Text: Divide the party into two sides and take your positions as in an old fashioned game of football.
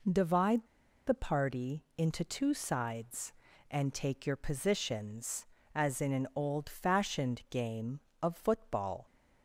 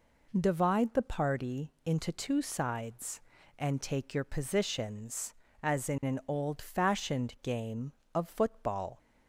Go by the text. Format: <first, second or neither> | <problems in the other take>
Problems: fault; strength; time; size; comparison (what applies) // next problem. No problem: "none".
second | pauses between "Divide" and "the"; at 0.6 s; 0.41 s long